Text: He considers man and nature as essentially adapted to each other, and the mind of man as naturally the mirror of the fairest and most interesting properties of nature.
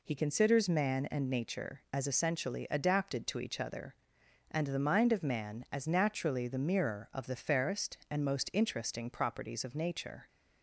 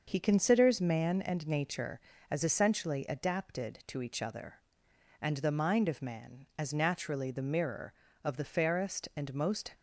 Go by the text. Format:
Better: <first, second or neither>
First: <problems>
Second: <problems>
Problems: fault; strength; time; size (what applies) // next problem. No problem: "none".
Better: first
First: none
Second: starts louder than the rest; until 1.0 s; 6 dB // stops before "interesting properties of nature"; at 9.7 s